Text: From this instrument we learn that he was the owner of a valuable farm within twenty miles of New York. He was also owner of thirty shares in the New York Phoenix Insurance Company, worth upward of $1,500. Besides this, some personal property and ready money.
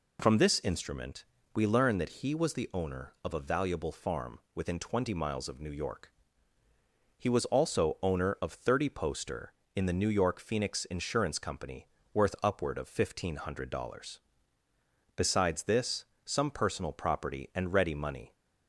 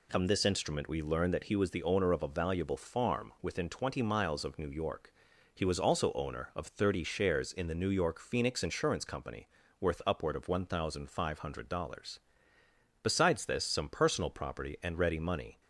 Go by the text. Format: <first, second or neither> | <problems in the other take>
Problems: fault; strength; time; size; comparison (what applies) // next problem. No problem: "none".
second | pauses between "instrument" and "we"; slight; at 1.2 s; 0.30 s long // pauses between "farm" and "within"; slight; at 4.3 s; 0.18 s long // says "poster" for "shares"; at 8.9 s